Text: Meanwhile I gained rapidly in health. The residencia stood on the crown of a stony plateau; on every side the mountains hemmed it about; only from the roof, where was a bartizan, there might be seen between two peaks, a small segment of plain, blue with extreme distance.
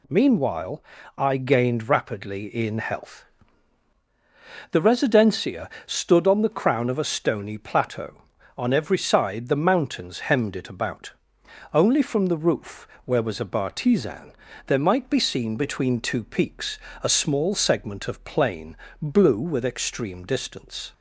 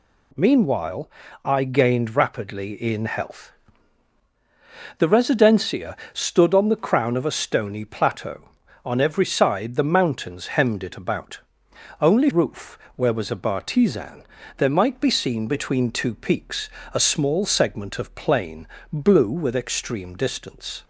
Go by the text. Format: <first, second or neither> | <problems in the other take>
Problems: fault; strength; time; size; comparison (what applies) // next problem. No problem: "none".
first | pauses between "Meanwhile" and "I"; slight; at 1.1 s; 0.34 s long; slight in the first // pauses between "residencia" and "stood"; slight; at 5.9 s; 0.16 s long; slight in the first // skips "from the"; at 12.3 s